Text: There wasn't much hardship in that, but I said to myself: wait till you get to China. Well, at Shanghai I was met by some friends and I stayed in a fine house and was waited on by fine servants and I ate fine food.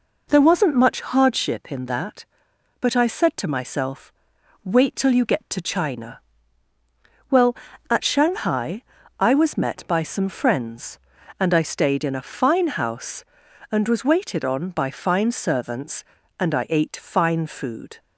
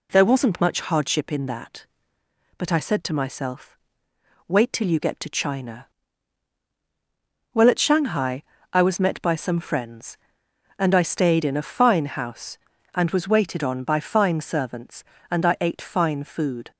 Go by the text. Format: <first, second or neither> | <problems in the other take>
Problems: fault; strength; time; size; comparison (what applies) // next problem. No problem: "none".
neither | pauses between "Shanghai" and "I"; slight; the same in both